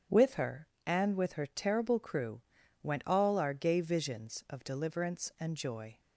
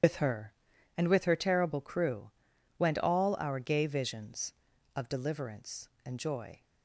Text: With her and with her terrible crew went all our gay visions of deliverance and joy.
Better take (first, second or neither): first